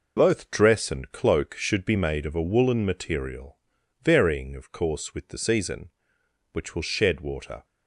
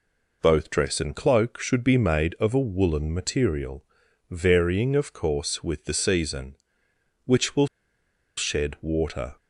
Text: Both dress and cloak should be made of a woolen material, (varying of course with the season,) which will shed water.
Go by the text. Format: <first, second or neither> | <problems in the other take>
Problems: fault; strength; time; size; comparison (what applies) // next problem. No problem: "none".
first | pauses between "will" and "shed"; noticeable; at 7.6 s; 0.69 s long